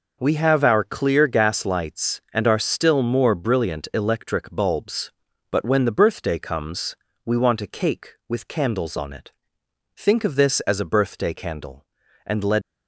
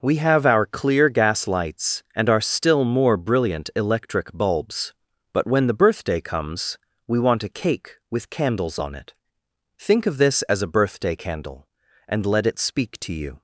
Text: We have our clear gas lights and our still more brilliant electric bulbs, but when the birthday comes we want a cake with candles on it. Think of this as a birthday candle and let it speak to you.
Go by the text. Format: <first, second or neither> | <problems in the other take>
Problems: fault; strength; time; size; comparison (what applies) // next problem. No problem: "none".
second | pauses between "comes" and "we"; slight; at 6.9 s; 0.28 s long; slight in the second // stops before "it speak to you"; at 12.6 s